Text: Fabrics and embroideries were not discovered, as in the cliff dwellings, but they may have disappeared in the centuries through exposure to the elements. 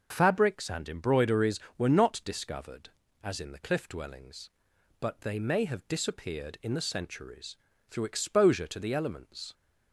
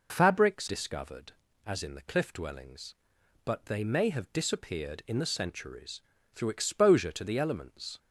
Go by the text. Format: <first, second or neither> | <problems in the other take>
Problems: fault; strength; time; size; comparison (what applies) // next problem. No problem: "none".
first | skips "and embroideries were not"; at 0.6 s // pauses between "centuries" and "through"; slight; at 6.0 s; 0.36 s long; slight in the first